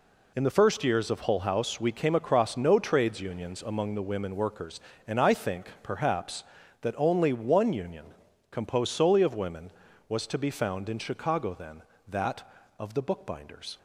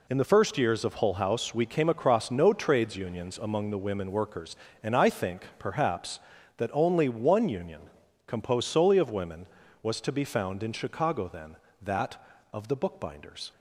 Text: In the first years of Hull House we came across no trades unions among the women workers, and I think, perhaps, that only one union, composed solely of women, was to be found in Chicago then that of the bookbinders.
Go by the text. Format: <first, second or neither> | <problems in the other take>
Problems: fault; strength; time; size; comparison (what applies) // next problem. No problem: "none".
neither | none